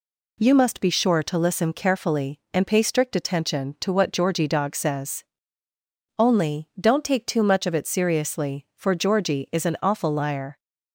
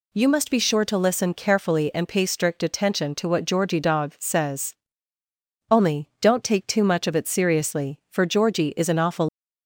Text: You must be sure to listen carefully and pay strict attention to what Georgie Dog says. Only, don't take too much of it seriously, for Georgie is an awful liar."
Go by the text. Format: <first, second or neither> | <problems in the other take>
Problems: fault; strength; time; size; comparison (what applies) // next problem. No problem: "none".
first | stops before "liar"; at 9.2 s